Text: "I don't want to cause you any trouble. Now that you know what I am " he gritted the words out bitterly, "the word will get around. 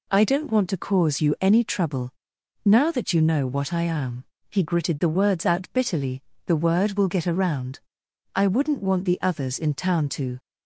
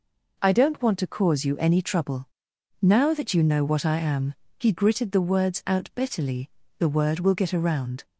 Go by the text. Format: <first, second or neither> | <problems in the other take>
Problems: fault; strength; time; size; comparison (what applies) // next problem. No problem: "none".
second | goes on to say "I wouldn't want the others in town to"; strong; from 8.3 s on; 2.0 s long